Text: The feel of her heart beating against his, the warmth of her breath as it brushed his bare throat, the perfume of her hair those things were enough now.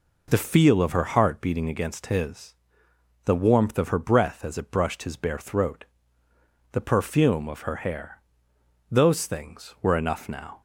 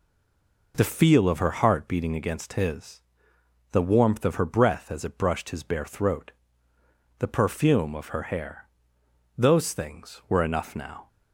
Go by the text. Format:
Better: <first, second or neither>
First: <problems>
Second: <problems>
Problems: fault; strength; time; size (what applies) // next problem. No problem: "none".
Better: first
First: pauses between "hair" and "those"; noticeable; at 8.1 s; 0.74 s long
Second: stays silent before the first word; slight; until 0.7 s; 0.7 s long // pauses between "hair" and "those"; noticeable; at 8.6 s; 0.74 s long